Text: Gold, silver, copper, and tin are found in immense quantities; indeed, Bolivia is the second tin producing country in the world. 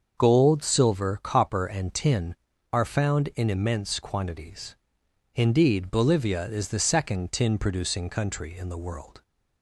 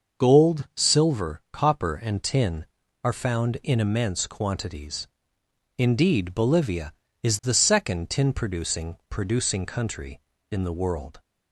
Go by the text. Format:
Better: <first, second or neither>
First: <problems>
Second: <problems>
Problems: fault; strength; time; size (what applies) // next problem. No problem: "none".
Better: first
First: starts louder than the rest; until 1.2 s; 6.5 dB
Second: starts louder than the rest; until 1.2 s; 6 dB // says "producing" twice; at 9.0 s